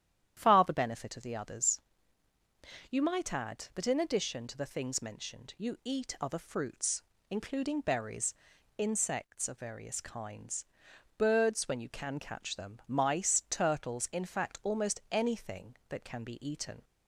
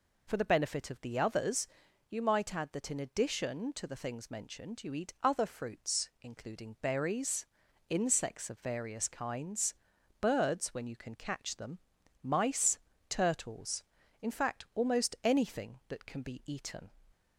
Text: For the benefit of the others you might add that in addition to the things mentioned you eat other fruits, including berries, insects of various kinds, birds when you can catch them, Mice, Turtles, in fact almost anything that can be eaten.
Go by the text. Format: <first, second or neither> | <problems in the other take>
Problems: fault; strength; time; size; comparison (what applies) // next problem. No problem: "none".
second | starts louder than the rest; strong; until 1.3 s; 10.5 dB // says "Far" for "For"; at 0.3 s // pauses between "others" and "you"; at 1.7 s; 1.1 s long; also in the second